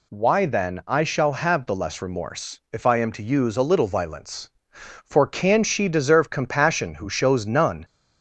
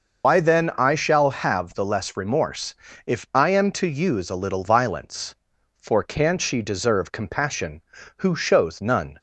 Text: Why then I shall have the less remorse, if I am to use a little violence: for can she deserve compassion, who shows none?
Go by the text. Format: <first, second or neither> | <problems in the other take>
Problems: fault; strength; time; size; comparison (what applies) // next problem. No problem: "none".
first | loses the start of "Why"; at 0.2 s; 80 ms